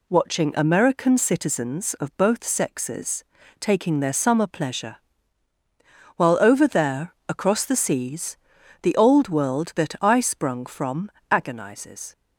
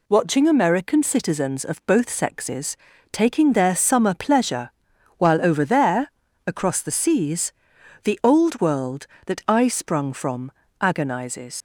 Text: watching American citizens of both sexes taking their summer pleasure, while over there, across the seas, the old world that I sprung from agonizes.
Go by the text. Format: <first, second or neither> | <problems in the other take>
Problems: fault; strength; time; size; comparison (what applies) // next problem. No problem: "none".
first | pauses between "sexes" and "taking"; slight; at 2.7 s; 0.36 s long; slight in the first // pauses between "from" and "agonizes"; slight; at 10.5 s; 0.30 s long; slight in the first // leaves "agonizes" unfinished; at 11.5 s; 80 ms